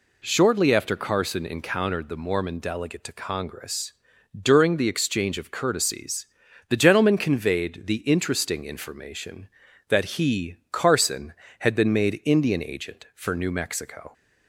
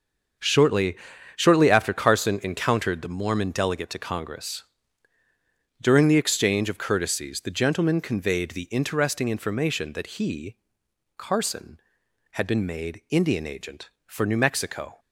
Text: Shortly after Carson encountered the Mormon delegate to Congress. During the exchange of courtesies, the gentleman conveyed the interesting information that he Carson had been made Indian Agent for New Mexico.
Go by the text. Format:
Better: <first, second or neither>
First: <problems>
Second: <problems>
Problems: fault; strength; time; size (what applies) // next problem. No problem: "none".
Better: first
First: pauses between "he" and "Carson"; slight; at 10.5 s; 0.16 s long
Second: starts louder than the rest; until 1.7 s; 6.5 dB // says "Shortly" twice; at 1.3 s // pauses between "he" and "Carson"; noticeable; at 10.5 s; 0.60 s long